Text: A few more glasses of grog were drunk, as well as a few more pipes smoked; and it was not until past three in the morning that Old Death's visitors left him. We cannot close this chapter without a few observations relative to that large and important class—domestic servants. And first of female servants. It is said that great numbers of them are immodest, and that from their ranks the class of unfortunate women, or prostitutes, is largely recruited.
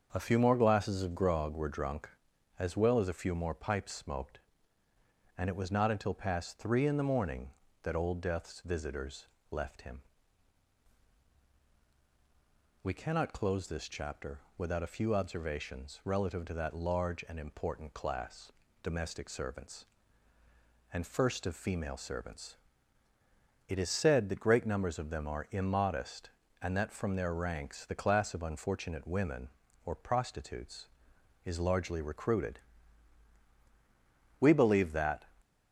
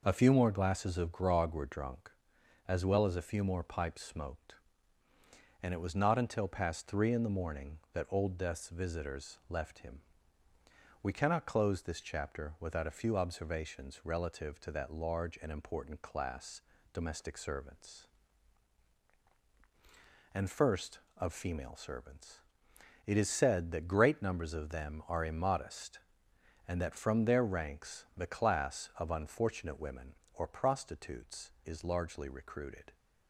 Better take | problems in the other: second | starts louder than the rest; until 1.1 s; 7 dB // pauses between "visitors" and "left"; slight; at 9.2 s; 0.24 s long // pauses between "chapter" and "without"; slight; at 14.3 s; 0.18 s long // goes on to say "We believe that"; noticeable; from 34.3 s on; 0.92 s long

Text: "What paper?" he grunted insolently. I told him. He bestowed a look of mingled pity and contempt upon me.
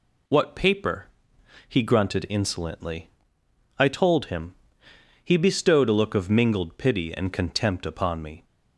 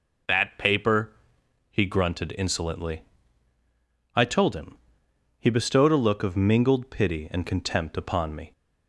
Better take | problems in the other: first | says "That" for "What"; at 0.2 s

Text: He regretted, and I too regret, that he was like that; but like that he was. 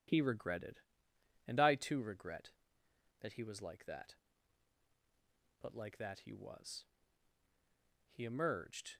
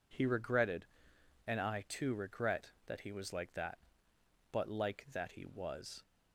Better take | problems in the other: second | goes on to say "He emerged"; noticeable; from 8.0 s on; 0.88 s long

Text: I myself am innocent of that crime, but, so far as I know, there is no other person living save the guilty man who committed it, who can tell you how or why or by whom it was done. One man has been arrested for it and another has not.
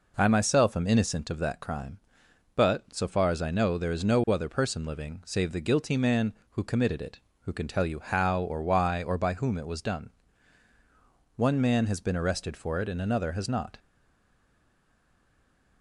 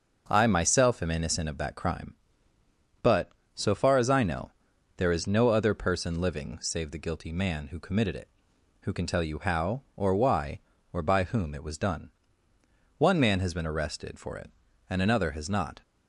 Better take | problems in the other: second | stays silent after the last word; noticeable; from 13.7 s on; 2.1 s long

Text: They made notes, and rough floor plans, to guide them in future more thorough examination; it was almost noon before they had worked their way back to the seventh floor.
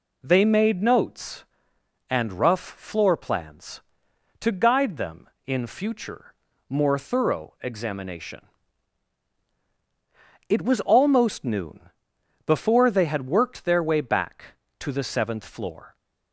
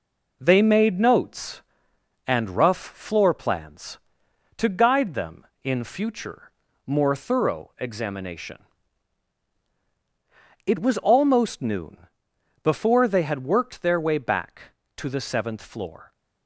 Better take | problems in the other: first | gets quieter; noticeable; throughout; 5 dB // pauses between "future" and "more"; slight; at 6.5 s; 0.36 s long; slight in the first // pauses between "noon" and "before"; noticeable; at 12.0 s; 0.56 s long; noticeable in the first

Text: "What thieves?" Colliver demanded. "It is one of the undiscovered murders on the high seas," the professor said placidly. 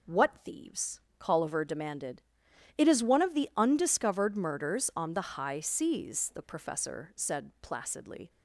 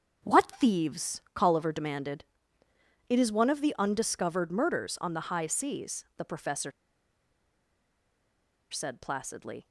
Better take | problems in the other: first | starts louder than the rest; strong; until 1.3 s; 7.5 dB // pauses between "professor" and "said"; strong; at 6.7 s; 1.9 s long

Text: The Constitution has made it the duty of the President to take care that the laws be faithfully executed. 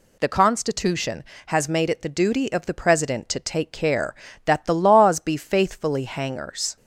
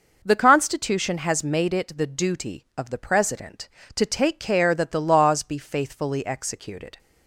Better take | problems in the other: second | says "hangers" for "executed"; at 6.0 s

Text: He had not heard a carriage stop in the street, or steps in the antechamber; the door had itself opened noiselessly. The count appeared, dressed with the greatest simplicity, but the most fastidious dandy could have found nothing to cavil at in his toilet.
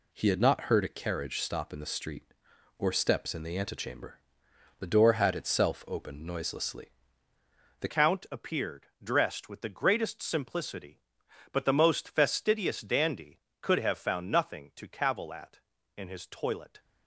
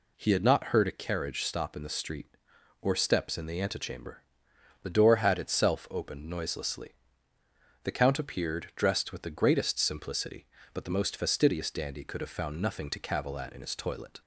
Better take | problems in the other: second | changes voice at "count"; from 7.8 s on; 8.9 s long

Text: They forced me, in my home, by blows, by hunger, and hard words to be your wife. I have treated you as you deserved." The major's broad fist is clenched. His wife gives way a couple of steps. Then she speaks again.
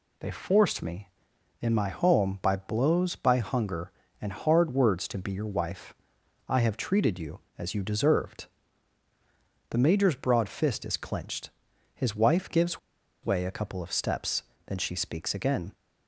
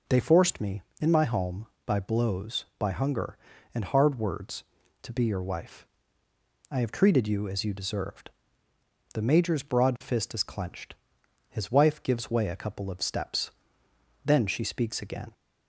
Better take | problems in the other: second | pauses between "gives" and "way"; at 12.7 s; 0.45 s long

